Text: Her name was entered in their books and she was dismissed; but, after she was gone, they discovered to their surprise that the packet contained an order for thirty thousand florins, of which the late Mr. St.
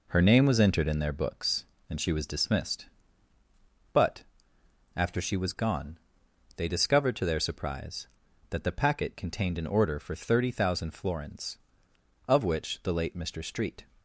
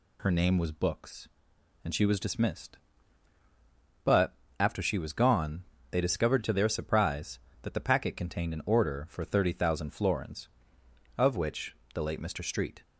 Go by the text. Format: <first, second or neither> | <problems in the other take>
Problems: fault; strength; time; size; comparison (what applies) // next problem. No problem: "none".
first | skips "entered in their"; at 0.7 s // pauses between "which" and "the"; slight; at 11.7 s; 0.20 s long